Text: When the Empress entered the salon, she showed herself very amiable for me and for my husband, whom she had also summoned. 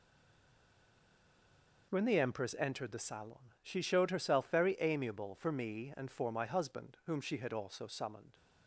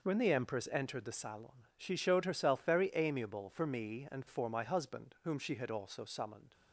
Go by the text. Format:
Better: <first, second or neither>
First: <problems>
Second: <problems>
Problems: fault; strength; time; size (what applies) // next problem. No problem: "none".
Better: second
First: stays silent before the first word; noticeable; until 1.8 s; 1.8 s long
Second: none